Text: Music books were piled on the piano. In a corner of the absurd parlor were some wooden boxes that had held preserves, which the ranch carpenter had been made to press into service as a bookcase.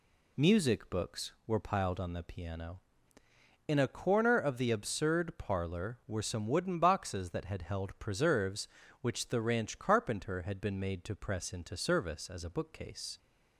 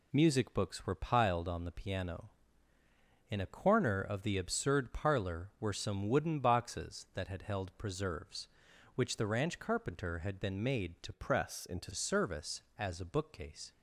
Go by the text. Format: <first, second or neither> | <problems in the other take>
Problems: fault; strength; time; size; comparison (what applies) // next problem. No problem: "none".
first | changes voice from "press" to "into"; from 11.1 to 11.9 s; 0.8 s long